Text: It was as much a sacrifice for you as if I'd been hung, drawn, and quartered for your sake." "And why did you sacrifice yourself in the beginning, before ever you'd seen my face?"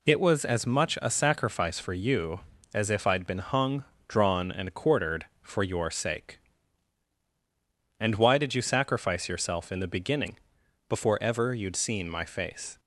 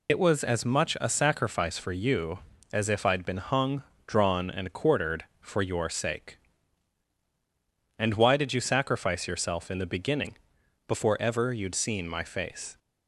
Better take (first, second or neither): first